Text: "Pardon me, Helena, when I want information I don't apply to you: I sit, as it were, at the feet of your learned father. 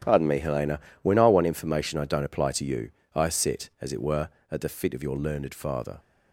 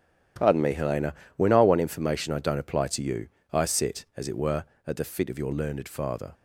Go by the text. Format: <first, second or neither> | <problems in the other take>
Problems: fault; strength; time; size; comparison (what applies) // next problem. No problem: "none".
neither | starts louder than the rest; strong; the same in both